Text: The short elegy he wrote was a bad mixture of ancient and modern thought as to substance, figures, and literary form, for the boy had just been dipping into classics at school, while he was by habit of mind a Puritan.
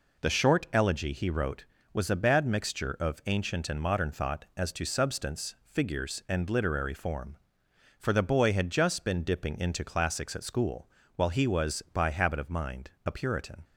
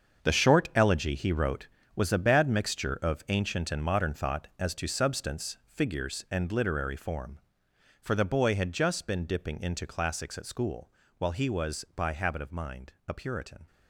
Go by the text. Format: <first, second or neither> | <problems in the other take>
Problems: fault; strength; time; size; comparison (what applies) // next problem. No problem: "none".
first | gets quieter; strong; throughout; 12 dB // pauses between "mind" and "a"; slight; at 12.9 s; 0.16 s long; slight in the first